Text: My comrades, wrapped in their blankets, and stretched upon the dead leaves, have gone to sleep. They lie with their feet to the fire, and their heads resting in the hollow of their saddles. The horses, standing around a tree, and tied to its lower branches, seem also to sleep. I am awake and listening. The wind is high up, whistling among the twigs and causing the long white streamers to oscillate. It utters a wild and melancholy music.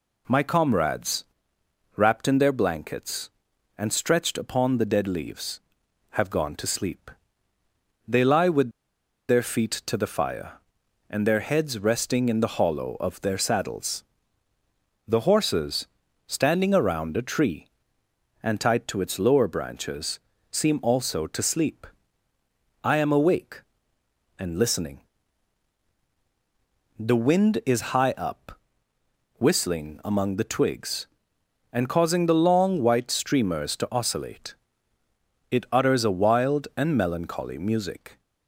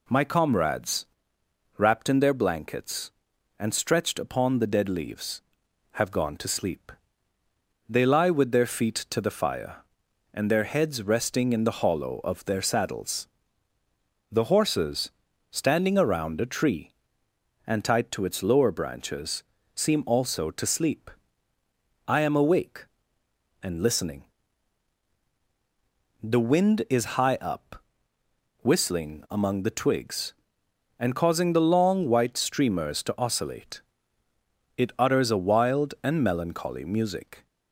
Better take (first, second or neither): second